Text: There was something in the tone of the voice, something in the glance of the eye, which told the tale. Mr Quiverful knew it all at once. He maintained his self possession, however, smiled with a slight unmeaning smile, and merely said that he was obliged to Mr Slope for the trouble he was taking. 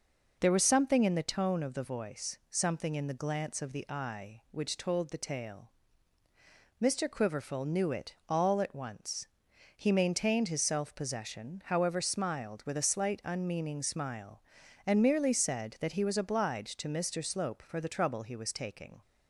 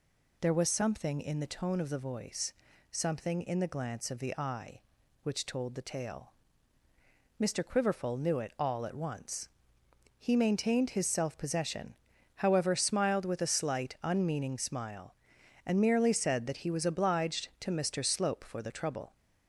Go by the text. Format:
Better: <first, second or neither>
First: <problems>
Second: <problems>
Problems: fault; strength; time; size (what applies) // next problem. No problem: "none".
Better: first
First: none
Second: stops before "he was taking"; at 19.1 s